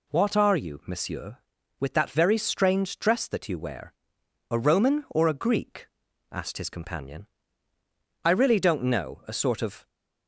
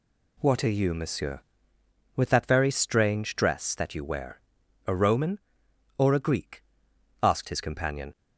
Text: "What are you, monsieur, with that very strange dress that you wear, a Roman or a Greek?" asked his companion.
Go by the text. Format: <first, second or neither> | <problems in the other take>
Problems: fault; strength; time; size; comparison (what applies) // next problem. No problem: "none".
second | goes on to say "I really don't know a sort of"; from 8.2 s on; 1.6 s long